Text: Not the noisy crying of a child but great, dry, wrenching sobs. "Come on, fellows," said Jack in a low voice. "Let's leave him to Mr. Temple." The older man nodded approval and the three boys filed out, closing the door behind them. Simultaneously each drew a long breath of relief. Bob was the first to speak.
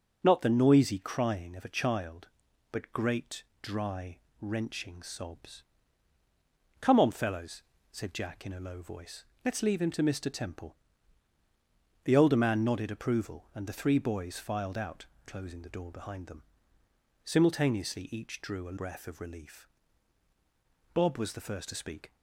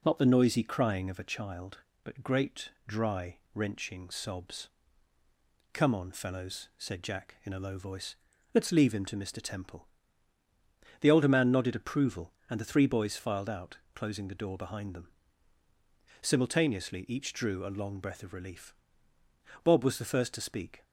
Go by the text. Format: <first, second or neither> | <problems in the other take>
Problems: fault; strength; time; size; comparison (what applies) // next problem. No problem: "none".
second | starts louder than the rest; until 1.2 s; 7 dB // skips "long"; at 18.7 s